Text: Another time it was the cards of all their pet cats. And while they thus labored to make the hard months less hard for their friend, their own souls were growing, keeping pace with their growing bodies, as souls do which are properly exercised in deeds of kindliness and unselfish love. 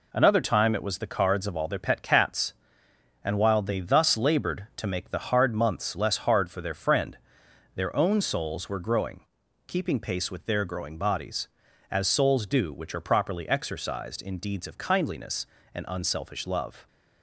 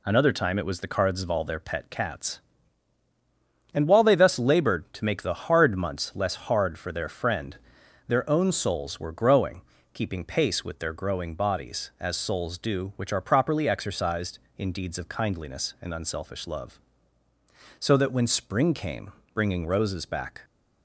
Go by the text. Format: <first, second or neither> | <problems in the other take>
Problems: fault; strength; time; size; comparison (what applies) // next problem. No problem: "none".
first | goes on to say "So that when spring came bringing roses back"; strong; from 17.7 s on; 2.6 s long